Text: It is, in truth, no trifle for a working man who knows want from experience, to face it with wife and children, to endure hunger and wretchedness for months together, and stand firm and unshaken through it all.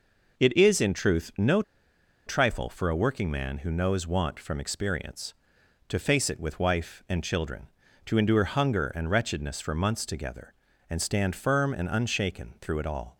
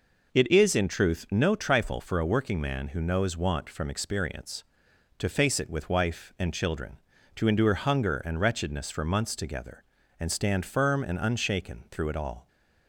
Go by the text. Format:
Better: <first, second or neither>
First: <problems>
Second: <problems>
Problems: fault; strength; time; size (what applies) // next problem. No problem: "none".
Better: second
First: pauses between "no" and "trifle"; noticeable; at 1.6 s; 0.64 s long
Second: none